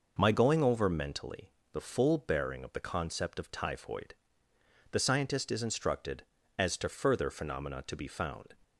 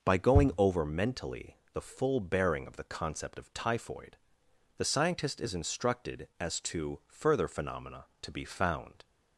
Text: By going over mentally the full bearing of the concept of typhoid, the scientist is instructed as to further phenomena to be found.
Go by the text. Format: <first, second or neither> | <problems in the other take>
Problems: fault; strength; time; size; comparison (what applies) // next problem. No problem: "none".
second | says "My" for "By"; at 0.1 s // pauses between "mentally" and "the"; slight; at 1.5 s; 0.22 s long; slight in the second